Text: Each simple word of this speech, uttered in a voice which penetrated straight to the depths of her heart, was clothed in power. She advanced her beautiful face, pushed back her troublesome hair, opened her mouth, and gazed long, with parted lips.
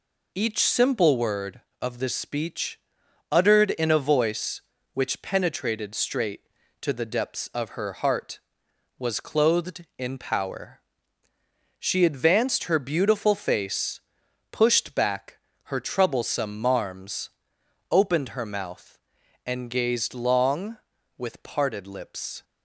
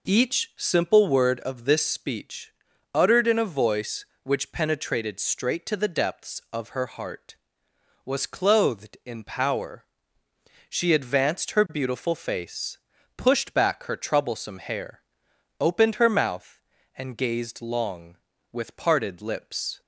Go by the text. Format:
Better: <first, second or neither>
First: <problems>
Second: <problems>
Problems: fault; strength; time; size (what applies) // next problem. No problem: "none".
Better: second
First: pauses between "back" and "her"; slight; at 15.3 s; 0.26 s long // says "marms" for "hair"; at 16.6 s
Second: none